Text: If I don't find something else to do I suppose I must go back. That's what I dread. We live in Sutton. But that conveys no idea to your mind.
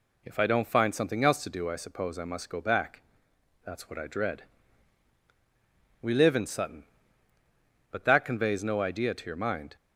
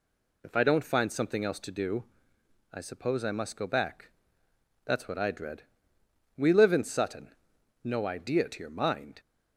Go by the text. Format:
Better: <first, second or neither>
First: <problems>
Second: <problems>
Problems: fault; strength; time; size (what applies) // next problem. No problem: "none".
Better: first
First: none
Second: pauses between "do" and "I"; noticeable; at 2.0 s; 0.68 s long // skips "But that conveys"; at 7.5 s